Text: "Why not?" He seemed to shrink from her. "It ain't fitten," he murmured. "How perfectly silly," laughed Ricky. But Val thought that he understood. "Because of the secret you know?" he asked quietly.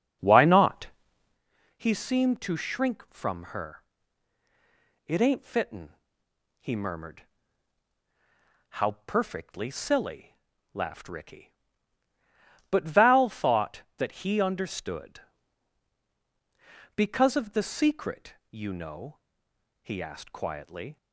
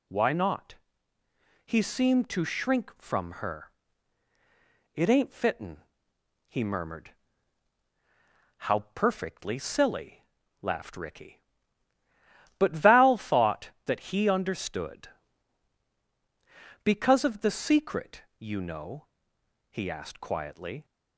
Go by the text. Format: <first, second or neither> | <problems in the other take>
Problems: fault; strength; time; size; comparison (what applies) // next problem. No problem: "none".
second | starts louder than the rest; until 1.4 s; 6.5 dB // pauses between "secret" and "you"; slight; at 18.3 s; 0.16 s long; slight in the second